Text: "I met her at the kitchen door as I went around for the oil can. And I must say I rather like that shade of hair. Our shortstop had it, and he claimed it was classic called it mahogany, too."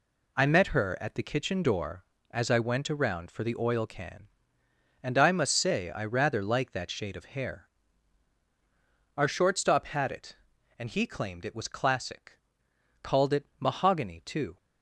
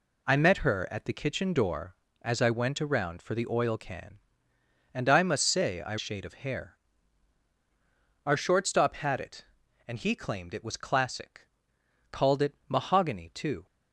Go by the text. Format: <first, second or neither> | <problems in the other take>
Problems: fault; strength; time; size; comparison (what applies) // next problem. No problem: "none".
first | skips "rather like that"; at 5.9 s // pauses between "classic" and "called"; noticeable; at 11.4 s; 0.64 s long; noticeable in the first